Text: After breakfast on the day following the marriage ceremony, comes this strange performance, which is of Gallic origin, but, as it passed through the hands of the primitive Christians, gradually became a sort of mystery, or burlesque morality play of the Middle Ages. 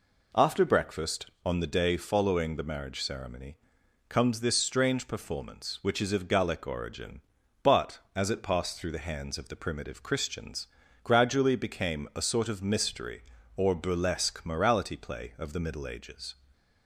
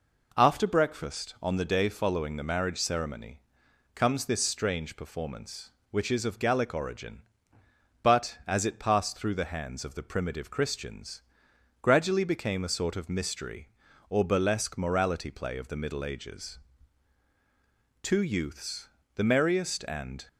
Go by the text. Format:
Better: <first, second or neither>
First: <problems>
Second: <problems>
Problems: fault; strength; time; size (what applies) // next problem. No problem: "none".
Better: first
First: none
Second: goes on to say "Two youths the merriest and"; strong; from 18.0 s on; 2.2 s long